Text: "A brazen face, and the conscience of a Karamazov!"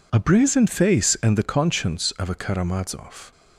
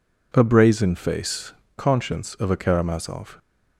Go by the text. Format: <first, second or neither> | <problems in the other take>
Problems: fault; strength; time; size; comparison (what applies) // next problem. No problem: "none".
first | skips "and the"; at 1.6 s